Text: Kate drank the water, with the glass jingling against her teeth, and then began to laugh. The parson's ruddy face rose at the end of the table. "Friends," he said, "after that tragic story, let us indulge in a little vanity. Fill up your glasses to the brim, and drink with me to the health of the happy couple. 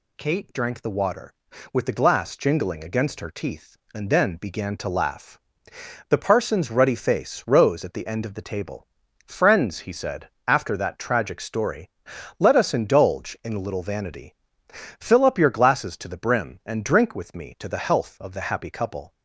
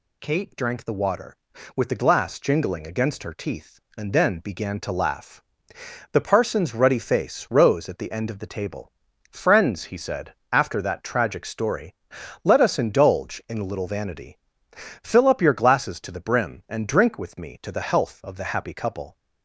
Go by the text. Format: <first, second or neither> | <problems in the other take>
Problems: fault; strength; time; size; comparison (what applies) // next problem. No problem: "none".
neither | none